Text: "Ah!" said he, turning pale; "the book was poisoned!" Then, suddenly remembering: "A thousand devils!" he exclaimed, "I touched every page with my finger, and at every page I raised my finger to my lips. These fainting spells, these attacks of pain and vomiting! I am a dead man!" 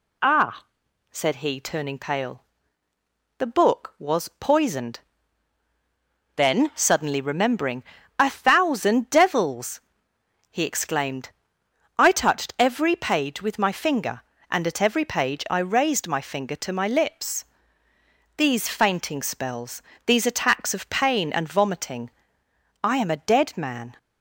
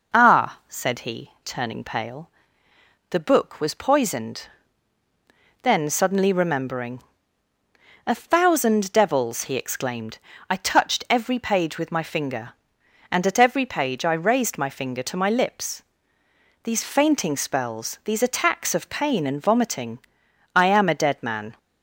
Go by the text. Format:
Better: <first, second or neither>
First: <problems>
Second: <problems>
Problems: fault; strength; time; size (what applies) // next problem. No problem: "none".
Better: neither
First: none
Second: none